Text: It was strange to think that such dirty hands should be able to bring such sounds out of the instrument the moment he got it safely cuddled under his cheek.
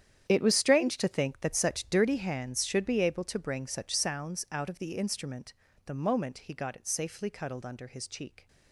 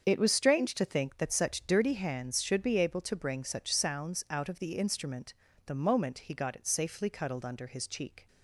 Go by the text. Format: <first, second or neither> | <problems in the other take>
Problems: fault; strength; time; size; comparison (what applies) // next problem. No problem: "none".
second | gets quieter; strong; throughout; 14.5 dB // starts louder than the rest; strong; until 1.2 s; 9.5 dB; also in the second // pauses between "instrument" and "the"; slight; at 5.5 s; 0.32 s long; slight in the second